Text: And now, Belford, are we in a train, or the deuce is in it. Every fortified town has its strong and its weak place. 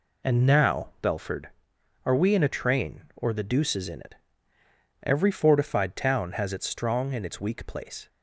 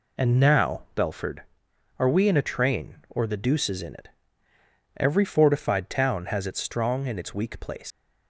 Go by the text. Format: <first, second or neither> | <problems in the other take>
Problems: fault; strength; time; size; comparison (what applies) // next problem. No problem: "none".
first | leaves "place" unfinished; at 7.9 s; 115 ms